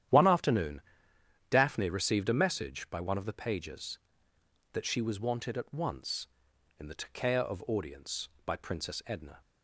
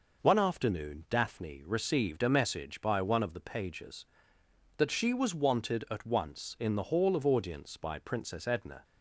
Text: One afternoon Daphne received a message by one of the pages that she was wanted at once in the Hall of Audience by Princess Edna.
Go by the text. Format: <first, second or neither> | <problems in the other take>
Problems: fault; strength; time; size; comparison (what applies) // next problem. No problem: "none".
second | starts louder than the rest; strong; until 1.8 s; 11 dB // pauses between "afternoon" and "Daphne"; noticeable; at 0.8 s; 0.70 s long // says "Takea" for "Hall"; at 6.9 s